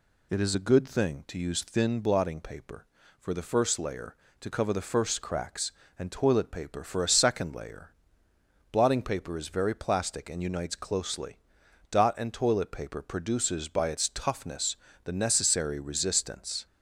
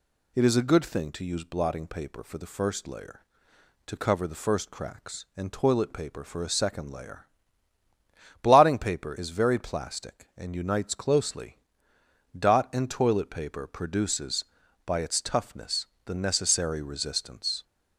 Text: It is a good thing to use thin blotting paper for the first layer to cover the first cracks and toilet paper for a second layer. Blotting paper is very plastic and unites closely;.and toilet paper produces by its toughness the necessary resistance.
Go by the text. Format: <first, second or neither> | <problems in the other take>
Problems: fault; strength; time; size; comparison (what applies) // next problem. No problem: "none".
first | skips "thin"; at 1.4 s // pauses between "toughness" and "the"; slight; at 15.8 s; 0.18 s long; slight in the first